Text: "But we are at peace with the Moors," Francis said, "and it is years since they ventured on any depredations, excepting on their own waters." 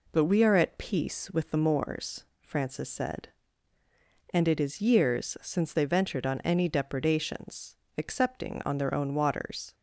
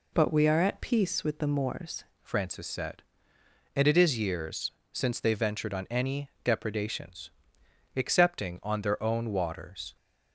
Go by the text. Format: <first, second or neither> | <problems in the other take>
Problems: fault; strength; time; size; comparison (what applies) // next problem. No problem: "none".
first | changes voice at "Francis"; from 2.2 s on; 7.7 s long // pauses between "years" and "since"; slight; at 4.6 s; 0.22 s long